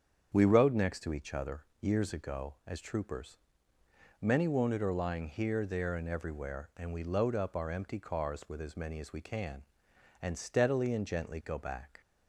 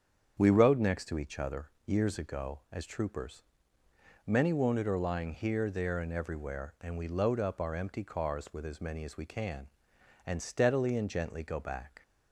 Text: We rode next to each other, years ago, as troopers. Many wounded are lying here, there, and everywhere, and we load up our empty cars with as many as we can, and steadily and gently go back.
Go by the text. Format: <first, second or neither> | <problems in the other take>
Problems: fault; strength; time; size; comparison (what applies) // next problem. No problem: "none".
neither | starts louder than the rest; strong; the same in both